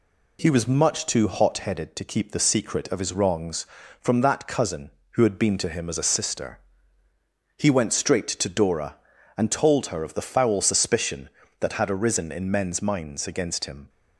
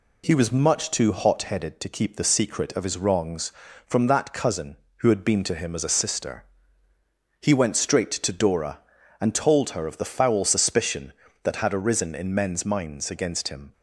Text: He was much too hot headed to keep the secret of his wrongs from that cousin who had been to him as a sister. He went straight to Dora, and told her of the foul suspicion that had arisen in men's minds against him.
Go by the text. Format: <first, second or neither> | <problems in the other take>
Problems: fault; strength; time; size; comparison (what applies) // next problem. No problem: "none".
neither | none